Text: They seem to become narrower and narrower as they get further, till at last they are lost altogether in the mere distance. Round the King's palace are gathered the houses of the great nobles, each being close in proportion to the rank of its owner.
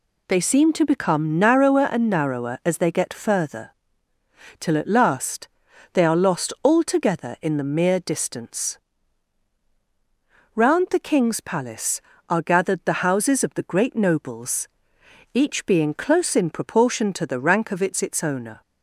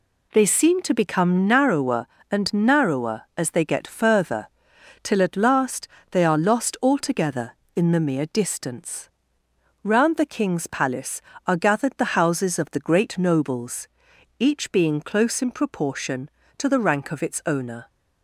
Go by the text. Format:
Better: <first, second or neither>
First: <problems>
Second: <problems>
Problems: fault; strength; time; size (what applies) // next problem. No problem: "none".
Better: second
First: pauses between "last" and "they"; noticeable; at 5.4 s; 0.46 s long // says "its" twice; at 18.0 s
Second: pauses between "last" and "they"; slight; at 5.8 s; 0.24 s long